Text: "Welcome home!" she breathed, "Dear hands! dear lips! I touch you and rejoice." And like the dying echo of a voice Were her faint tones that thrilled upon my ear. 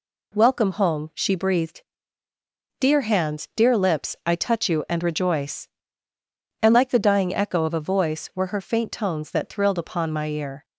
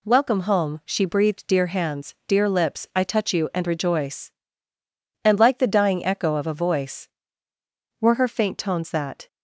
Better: first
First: none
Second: stops before "thrilled upon my ear"; at 9.2 s

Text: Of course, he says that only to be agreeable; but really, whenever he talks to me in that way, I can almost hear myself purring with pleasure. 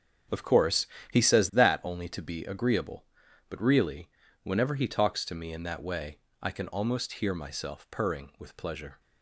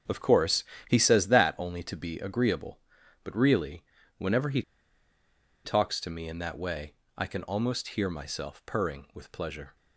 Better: first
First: starts louder than the rest; strong; until 1.6 s; 8.5 dB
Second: starts louder than the rest; strong; until 1.3 s; 8 dB // pauses between "he" and "talks"; at 4.6 s; 1.0 s long

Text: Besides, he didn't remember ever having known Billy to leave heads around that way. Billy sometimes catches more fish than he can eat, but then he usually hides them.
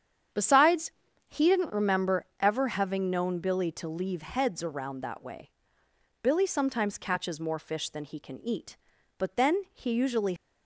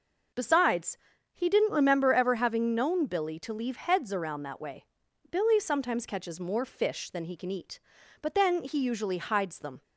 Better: second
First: starts louder than the rest; strong; until 1.7 s; 8.5 dB // pauses between "remember" and "ever"; slight; at 2.2 s; 0.16 s long // stops before "hides them"; at 10.3 s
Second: none

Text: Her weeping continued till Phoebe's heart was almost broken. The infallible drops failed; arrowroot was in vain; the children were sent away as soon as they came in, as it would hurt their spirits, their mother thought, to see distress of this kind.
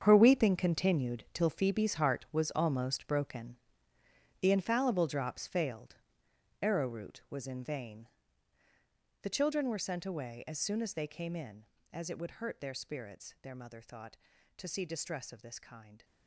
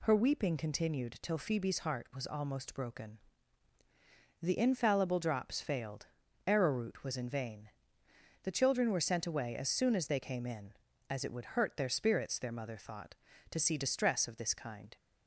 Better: second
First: gets quieter; strong; throughout; 13.5 dB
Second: none

